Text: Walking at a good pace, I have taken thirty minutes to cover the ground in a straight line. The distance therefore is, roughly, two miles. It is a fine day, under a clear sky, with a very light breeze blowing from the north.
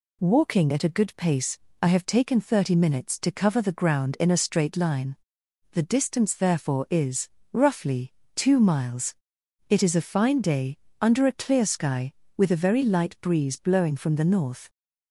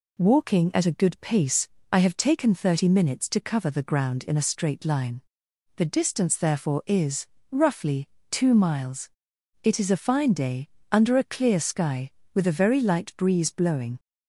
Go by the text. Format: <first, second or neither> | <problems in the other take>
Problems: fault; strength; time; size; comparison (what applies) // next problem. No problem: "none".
first | stops before "from the north"; at 13.9 s